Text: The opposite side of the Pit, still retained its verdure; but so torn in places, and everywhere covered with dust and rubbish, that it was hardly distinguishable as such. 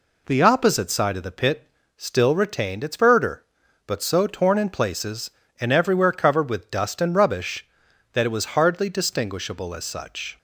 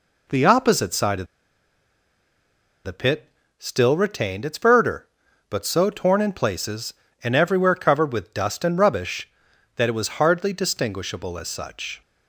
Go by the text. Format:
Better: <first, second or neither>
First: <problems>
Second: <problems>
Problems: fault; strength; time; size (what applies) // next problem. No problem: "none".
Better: first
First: none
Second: pauses between "of" and "the"; strong; at 1.2 s; 1.5 s long